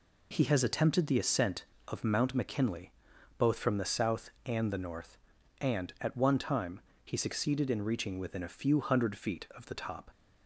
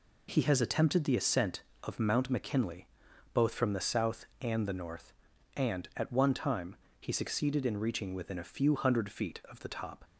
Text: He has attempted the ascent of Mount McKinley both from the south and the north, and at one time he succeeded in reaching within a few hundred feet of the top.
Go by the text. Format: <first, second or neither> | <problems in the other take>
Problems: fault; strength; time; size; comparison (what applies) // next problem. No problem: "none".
neither | pauses between "McKinley" and "both"; noticeable; the same in both // pauses between "time" and "he"; slight; the same in both